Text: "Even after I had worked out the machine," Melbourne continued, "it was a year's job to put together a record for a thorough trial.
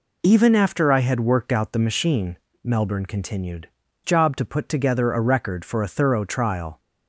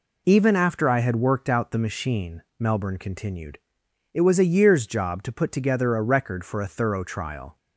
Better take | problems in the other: second | skips "it was a year's"; at 3.8 s

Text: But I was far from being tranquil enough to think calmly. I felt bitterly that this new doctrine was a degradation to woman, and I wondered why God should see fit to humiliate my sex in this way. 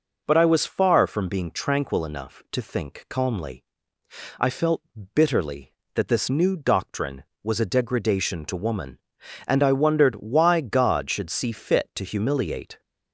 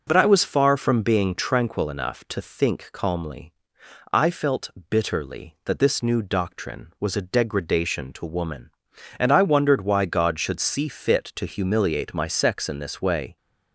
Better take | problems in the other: second | pauses between "felt" and "bitterly"; slight; at 4.8 s; 0.32 s long; slight in the second // stops before "my sex in this way"; at 12.8 s

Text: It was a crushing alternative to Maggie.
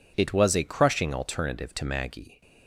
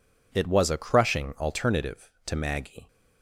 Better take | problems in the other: neither | none

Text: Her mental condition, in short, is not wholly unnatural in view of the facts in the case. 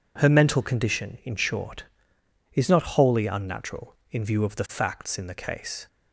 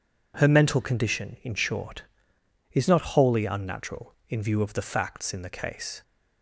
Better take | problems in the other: neither | none

